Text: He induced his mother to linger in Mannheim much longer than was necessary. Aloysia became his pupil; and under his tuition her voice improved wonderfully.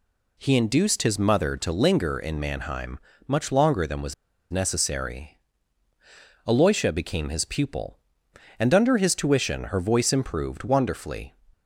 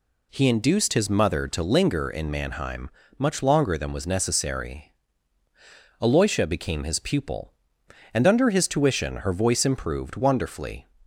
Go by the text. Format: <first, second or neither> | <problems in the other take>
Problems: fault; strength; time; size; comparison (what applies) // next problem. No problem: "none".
second | pauses between "Mannheim" and "much"; slight; at 3.0 s; 0.26 s long; slight in the second // pauses between "was" and "necessary"; at 4.1 s; 0.36 s long